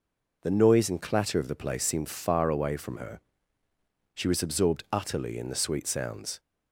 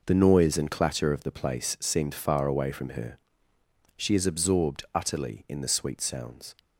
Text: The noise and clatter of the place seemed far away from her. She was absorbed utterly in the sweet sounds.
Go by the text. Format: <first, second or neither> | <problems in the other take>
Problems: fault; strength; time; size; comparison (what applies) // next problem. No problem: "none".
first | says "is" for "was"; at 4.1 s